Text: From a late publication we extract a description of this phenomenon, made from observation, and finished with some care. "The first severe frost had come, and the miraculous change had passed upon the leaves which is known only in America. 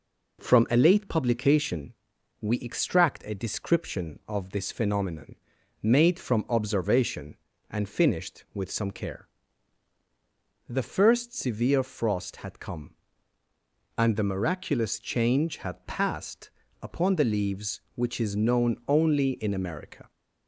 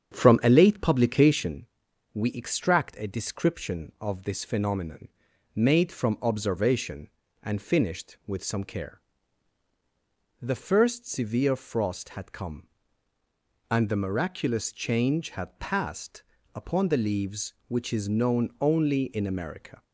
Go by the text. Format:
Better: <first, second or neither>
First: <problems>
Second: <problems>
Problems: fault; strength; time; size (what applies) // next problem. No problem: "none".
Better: first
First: pauses between "publication" and "we"; noticeable; at 1.9 s; 0.48 s long // pauses between "passed" and "upon"; slight; at 16.4 s; 0.32 s long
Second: starts louder than the rest; strong; until 1.5 s; 8 dB // pauses between "publication" and "we"; noticeable; at 1.6 s; 0.48 s long // pauses between "passed" and "upon"; slight; at 16.2 s; 0.32 s long